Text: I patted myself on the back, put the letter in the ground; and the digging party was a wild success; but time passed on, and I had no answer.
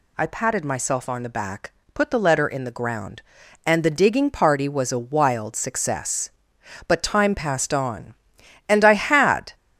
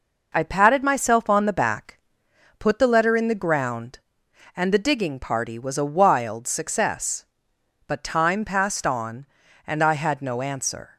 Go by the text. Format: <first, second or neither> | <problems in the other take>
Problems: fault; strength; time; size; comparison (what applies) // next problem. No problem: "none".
second | stops before "no answer"; at 9.5 s